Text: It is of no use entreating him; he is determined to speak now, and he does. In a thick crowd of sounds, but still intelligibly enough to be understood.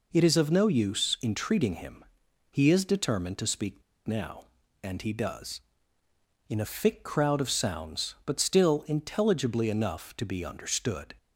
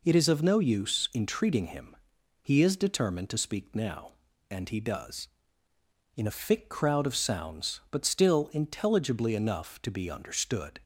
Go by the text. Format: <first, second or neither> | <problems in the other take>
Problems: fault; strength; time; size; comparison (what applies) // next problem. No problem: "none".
second | pauses between "speak" and "now"; slight; at 3.8 s; 0.25 s long